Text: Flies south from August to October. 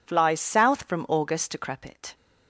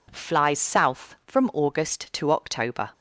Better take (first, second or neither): second